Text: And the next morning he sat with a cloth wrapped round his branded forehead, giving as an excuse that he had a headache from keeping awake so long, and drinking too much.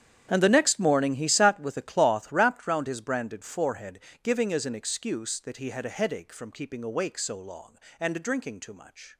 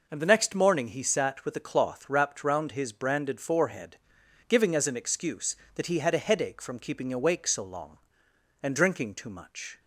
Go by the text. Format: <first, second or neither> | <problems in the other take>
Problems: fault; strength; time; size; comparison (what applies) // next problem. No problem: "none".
second | gets quieter; strong; throughout; 16 dB